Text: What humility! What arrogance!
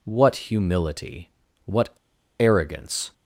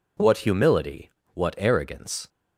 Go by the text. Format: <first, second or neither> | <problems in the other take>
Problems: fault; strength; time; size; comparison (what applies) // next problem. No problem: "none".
second | pauses between "What" and "arrogance"; noticeable; at 1.8 s; 0.49 s long